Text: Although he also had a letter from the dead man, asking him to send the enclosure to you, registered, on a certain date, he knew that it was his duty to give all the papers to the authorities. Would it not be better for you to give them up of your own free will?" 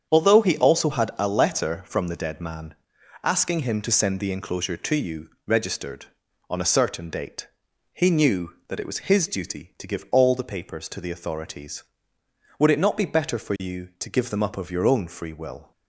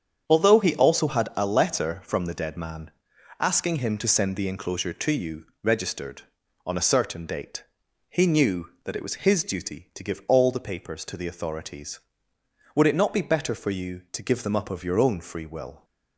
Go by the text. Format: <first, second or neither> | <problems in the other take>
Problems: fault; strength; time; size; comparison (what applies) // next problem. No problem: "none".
neither | starts louder than the rest; strong; the same in both